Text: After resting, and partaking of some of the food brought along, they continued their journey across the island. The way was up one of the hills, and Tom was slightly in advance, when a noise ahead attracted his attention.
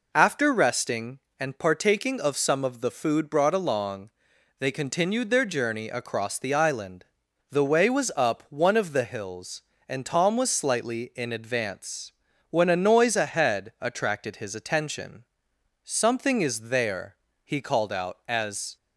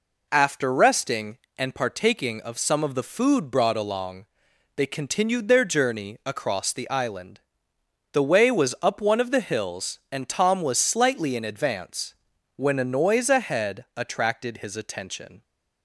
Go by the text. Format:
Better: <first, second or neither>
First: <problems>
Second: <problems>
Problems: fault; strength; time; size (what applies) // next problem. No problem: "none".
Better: second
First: goes on to say "Something is there he called out as"; strong; from 15.8 s on; 2.9 s long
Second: none